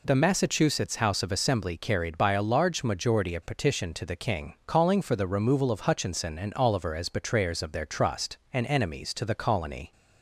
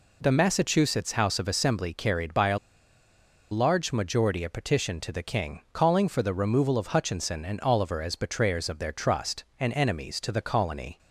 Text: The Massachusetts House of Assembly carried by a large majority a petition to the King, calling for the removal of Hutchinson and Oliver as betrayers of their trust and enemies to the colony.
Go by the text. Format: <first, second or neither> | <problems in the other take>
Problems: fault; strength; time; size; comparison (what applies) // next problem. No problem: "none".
first | pauses between "a" and "large"; noticeable; at 2.5 s; 0.93 s long